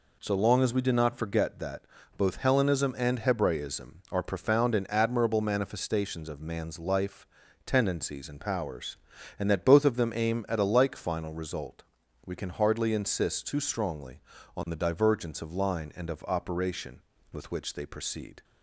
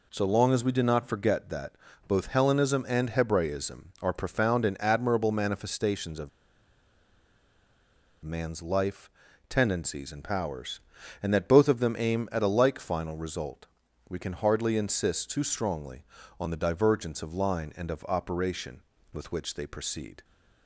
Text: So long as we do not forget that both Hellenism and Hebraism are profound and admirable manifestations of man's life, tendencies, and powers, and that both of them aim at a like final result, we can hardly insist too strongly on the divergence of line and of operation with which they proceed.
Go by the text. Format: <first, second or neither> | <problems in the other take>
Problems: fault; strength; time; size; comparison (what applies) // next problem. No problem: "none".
first | pauses between "that" and "both"; slight; at 1.7 s; 0.34 s long; slight in the first // pauses between "of" and "man's"; strong; at 6.2 s; 1.9 s long